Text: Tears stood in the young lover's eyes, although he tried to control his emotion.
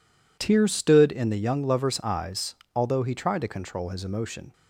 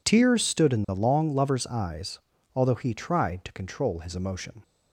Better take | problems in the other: first | says "long" for "young"; at 0.9 s

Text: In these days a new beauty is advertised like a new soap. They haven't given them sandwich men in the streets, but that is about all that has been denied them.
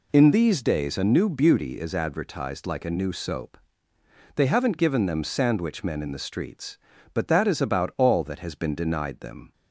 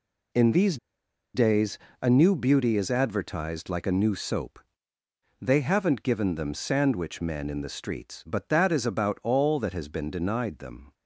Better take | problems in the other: first | pauses between "these" and "days"; noticeable; at 0.7 s; 0.56 s long // pauses between "days" and "a"; slight; at 1.7 s; 0.24 s long

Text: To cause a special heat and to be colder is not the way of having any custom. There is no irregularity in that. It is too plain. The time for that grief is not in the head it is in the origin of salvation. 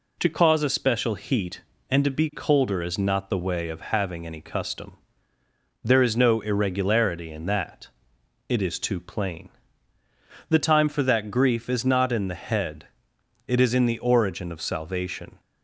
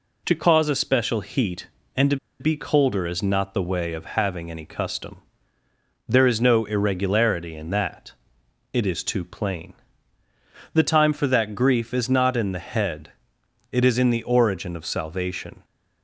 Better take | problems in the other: first | pauses between "to" and "be"; slight; at 2.1 s; 0.23 s long // pauses between "head" and "it"; noticeable; at 13.1 s; 0.60 s long; noticeable in the first

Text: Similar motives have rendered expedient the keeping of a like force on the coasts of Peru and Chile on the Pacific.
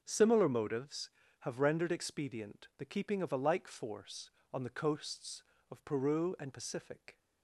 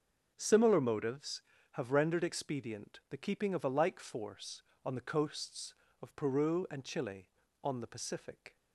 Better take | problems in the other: second | starts louder than the rest; until 1.0 s; 6.5 dB; also in the second // skips "Chile on the"; at 6.5 s

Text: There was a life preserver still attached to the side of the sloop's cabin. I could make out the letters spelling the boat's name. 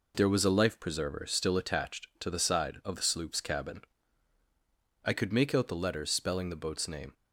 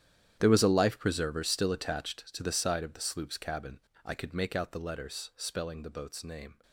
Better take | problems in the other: first | gets quieter; strong; throughout; 16.5 dB

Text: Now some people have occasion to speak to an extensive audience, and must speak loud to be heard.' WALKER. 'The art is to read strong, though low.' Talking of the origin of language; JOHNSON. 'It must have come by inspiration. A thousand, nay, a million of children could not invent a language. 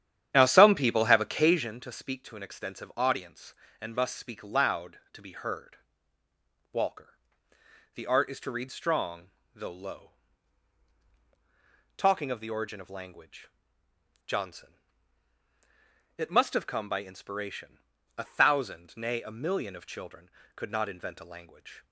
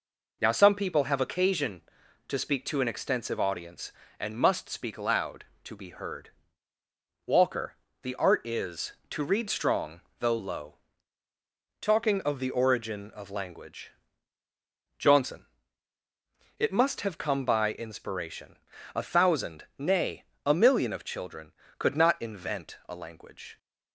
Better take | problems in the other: second | starts louder than the rest; strong; until 1.7 s; 10 dB

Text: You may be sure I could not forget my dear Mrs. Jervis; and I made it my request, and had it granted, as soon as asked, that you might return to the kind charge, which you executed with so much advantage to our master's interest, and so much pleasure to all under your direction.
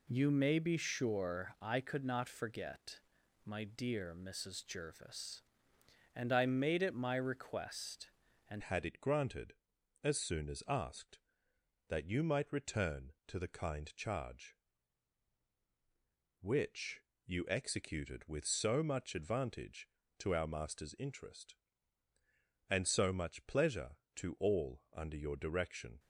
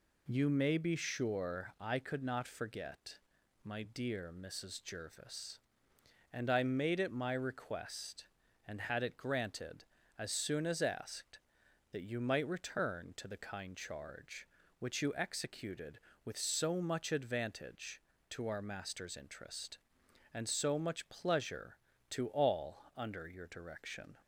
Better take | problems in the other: second | pauses between "forget" and "my"; at 3.0 s; 0.44 s long; also in the second // changes voice at "had"; from 8.6 s on; 17.3 s long // pauses between "which" and "you"; slight; at 17.0 s; 0.22 s long

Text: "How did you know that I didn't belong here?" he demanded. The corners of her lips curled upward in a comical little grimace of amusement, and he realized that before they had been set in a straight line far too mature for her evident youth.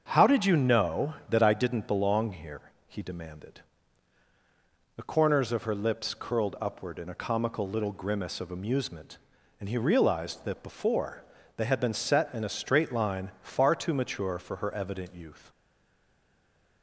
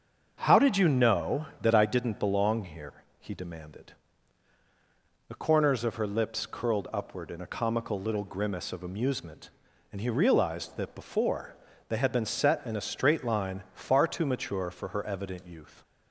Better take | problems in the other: second | starts louder than the rest; until 1.0 s; 7 dB; also in the second // pauses between "before" and "they"; slight; at 11.2 s; 0.32 s long; slight in the second // stays silent after the last word; noticeable; from 15.5 s on; 1.3 s long

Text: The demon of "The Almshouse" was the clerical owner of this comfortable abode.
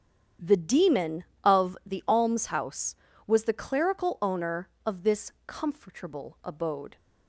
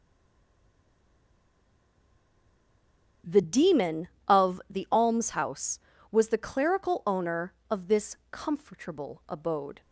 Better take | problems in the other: first | stays silent before the first word; strong; until 3.2 s; 3.2 s long // starts louder than the rest; strong; until 4.4 s; 9 dB; strong in the first // pauses between "this" and "comfortable"; slight; at 8.1 s; 0.16 s long; slight in the first

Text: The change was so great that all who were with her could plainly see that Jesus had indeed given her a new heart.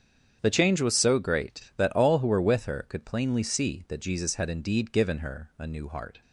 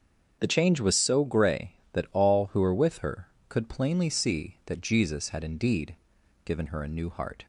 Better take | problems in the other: first | starts louder than the rest; until 1.3 s; 7 dB; strong in the first // says "grey" for "great"; at 1.2 s // pauses between "indeed" and "given"; noticeable; at 5.9 s; 0.50 s long

